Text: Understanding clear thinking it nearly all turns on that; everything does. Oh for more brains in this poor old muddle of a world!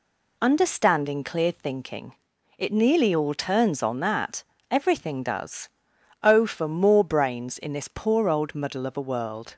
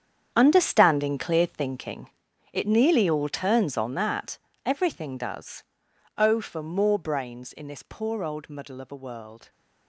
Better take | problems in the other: first | gets quieter; strong; throughout; 13.5 dB // pauses between "thinking" and "it"; noticeable; at 2.0 s; 0.46 s long; noticeable in the first

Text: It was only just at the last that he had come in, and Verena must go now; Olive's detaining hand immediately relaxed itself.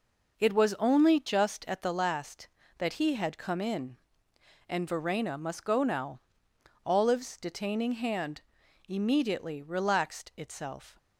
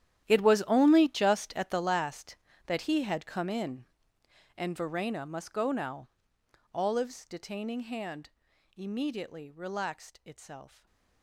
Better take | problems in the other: first | gets quieter; strong; throughout; 16.5 dB // pauses between "hand" and "immediately"; noticeable; at 8.2 s; 0.46 s long; noticeable in the first // stays silent after the last word; slight; from 10.6 s on; 0.6 s long

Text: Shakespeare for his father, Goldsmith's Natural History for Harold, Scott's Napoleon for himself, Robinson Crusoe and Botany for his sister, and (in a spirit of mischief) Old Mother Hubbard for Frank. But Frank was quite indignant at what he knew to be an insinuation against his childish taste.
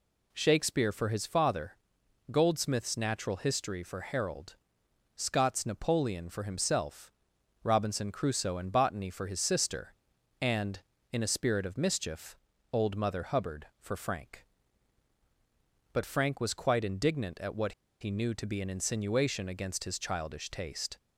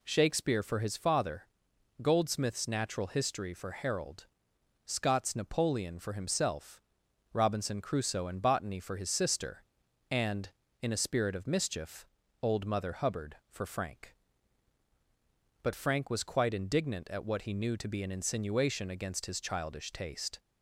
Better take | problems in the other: second | pauses between "what" and "he"; slight; at 17.7 s; 0.28 s long

